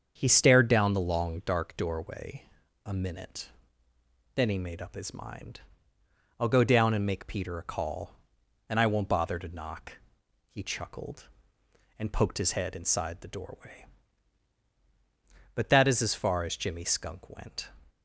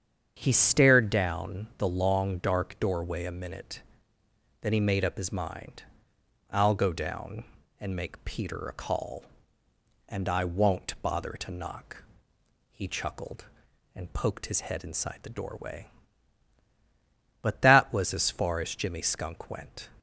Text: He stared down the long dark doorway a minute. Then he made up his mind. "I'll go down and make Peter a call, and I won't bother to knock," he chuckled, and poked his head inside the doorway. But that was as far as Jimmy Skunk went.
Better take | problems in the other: second | starts louder than the rest; strong; until 1.1 s; 7.5 dB; strong in the second // pauses between "doorway" and "a"; at 2.4 s; 0.42 s long // says "is" for "was"; at 15.8 s

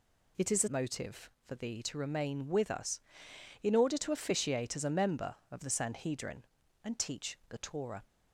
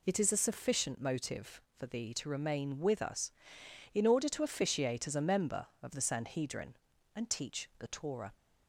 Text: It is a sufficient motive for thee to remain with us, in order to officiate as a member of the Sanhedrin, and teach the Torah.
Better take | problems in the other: second | skips "sufficient"; at 0.6 s

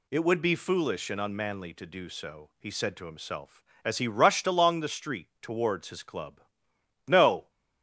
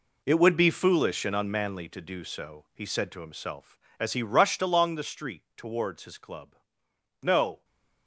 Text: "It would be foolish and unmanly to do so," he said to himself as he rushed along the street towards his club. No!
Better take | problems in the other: first | gets quieter; strong; throughout; 12 dB // stays silent after the last word; slight; from 7.5 s on; 0.5 s long

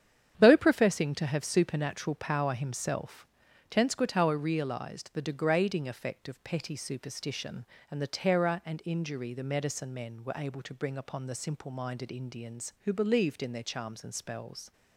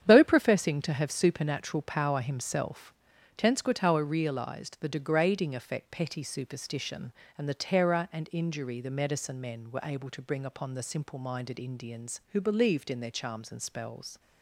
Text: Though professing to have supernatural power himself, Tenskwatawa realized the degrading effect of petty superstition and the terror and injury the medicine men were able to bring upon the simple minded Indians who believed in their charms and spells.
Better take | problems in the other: first | starts louder than the rest; strong; until 1.0 s; 9 dB; strong in the first // skips "of"; at 5.9 s

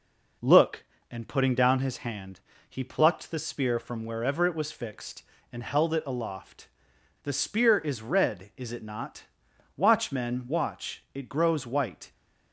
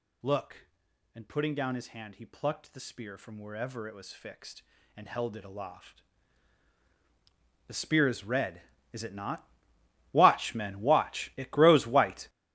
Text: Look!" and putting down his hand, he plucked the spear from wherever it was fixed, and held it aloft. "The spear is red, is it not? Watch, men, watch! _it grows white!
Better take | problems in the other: first | gets louder; strong; throughout; 12 dB

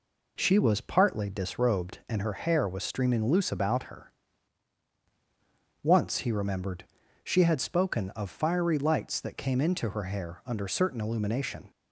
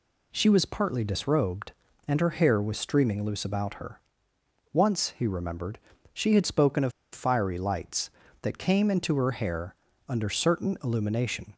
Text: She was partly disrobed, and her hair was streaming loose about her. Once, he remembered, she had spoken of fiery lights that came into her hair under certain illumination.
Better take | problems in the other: first | pauses between "of" and "fiery"; slight; at 6.9 s; 0.22 s long // pauses between "hair" and "under"; slight; at 9.7 s; 0.34 s long

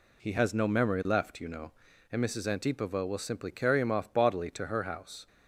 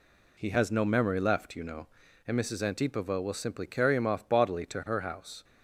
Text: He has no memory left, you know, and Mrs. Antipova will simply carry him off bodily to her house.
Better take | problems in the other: neither | none

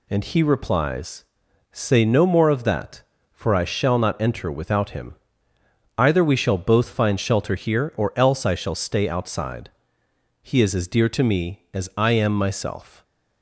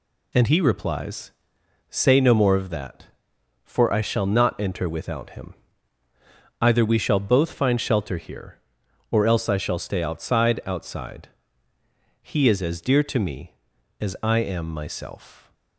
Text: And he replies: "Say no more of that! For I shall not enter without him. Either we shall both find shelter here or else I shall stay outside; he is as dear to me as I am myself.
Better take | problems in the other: first | says "outside" twice; at 10.6 s

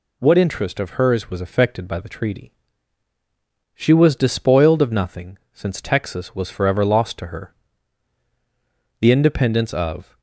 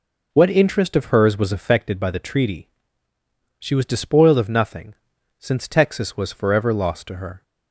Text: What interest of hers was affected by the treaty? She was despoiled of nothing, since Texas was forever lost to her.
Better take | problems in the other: second | goes on to say "The independence of"; noticeable; from 8.9 s on; 1.2 s long

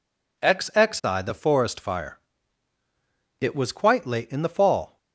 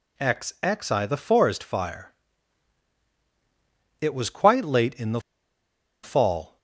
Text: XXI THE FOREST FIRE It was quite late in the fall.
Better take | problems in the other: first | pauses between "FIRE" and "It"; strong; at 2.1 s; 1.8 s long; also in the first // pauses between "the" and "fall"; noticeable; at 5.1 s; 0.83 s long

